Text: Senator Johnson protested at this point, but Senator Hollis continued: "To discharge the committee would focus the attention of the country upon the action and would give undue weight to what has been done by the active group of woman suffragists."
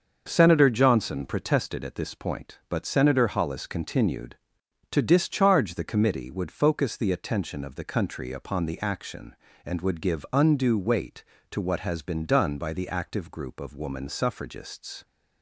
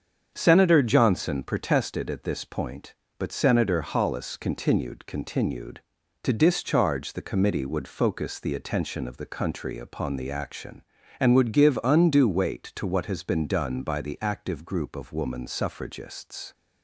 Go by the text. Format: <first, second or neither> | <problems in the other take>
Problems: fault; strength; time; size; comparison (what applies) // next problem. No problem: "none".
first | starts louder than the rest; strong; until 1.3 s; 7.5 dB; also in the first // says "continued" twice; at 5.0 s